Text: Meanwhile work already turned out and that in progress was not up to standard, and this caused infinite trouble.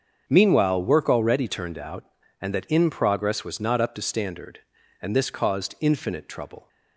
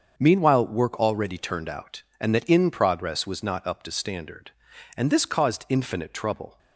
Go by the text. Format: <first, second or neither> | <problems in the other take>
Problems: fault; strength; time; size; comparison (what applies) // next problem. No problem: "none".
neither | starts louder than the rest; the same in both